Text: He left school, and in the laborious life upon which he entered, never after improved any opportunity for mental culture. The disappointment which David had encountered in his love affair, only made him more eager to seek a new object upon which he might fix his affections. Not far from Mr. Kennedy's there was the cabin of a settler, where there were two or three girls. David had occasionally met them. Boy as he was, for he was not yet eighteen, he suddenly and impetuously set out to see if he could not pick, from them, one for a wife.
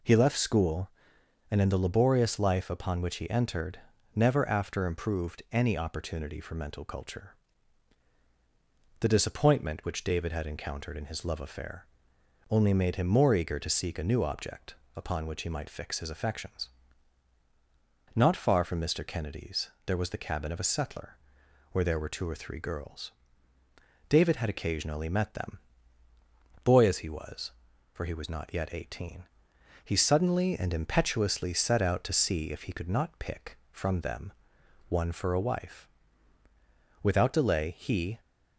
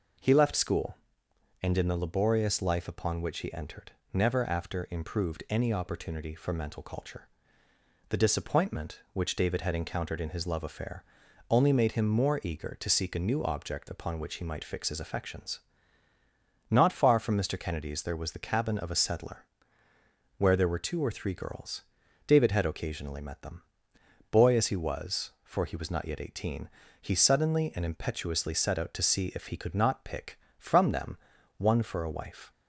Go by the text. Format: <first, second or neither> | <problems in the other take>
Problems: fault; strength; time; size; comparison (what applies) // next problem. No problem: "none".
second | pauses between "object" and "upon"; slight; at 14.7 s; 0.22 s long // pauses between "Kennedy's" and "there"; slight; at 19.6 s; 0.16 s long // goes on to say "Without delay he"; noticeable; from 37.0 s on; 1.1 s long